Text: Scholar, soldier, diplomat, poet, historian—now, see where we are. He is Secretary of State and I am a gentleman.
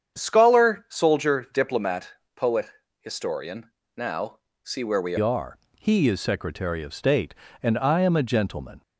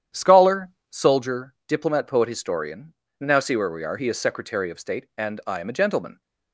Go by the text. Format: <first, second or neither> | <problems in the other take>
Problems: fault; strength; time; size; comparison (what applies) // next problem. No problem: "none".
second | starts louder than the rest; strong; until 1.2 s; 8 dB; strong in the second // changes voice at "are"; from 5.1 s on; 3.7 s long